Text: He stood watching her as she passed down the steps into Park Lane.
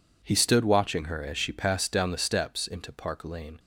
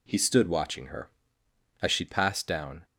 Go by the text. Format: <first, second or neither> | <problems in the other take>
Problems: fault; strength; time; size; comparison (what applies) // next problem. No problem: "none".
first | stops before "the steps into Park Lane"; at 2.8 s